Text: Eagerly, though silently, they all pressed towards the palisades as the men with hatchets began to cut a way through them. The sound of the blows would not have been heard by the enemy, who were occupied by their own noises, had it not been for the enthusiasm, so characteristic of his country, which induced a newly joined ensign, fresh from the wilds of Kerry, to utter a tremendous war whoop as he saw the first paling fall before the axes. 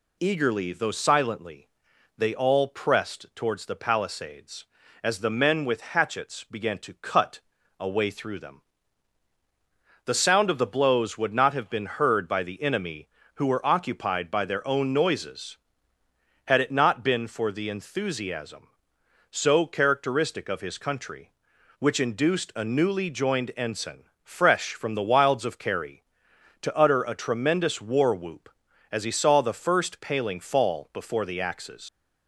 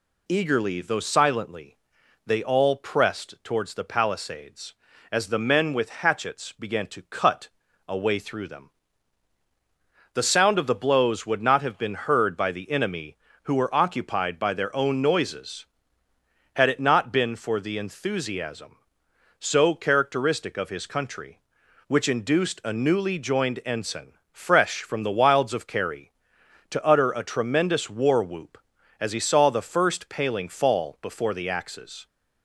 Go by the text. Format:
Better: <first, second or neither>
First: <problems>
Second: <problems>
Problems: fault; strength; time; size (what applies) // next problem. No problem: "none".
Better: second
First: pauses between "cut" and "a"; at 7.3 s; 0.40 s long // leaves "axes" unfinished; at 31.8 s; 90 ms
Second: pauses between "cut" and "a"; at 7.4 s; 0.40 s long